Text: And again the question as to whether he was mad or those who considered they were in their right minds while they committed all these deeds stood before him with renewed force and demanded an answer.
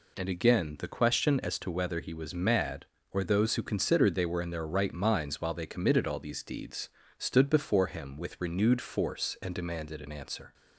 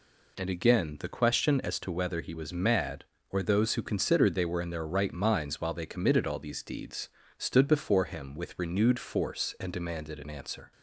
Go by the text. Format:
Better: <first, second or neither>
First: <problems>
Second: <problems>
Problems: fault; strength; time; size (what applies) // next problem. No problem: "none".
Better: neither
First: pauses between "deeds" and "stood"; slight; at 6.8 s; 0.28 s long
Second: pauses between "deeds" and "stood"; slight; at 7.0 s; 0.28 s long